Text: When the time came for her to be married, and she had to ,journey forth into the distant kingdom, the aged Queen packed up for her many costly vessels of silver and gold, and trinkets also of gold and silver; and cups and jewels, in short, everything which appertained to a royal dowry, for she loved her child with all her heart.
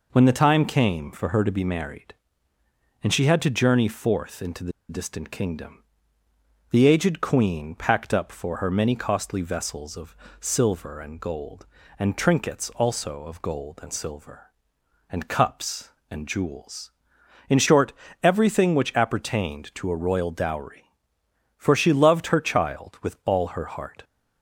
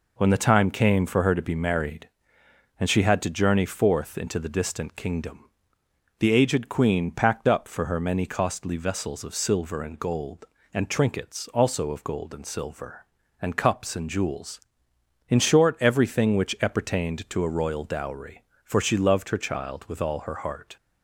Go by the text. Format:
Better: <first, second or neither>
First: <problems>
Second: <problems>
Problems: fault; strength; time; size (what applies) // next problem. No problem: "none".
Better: second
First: pauses between "the" and "distant"; slight; at 4.7 s; 0.18 s long // pauses between "of" and "silver"; slight; at 10.1 s; 0.24 s long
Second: none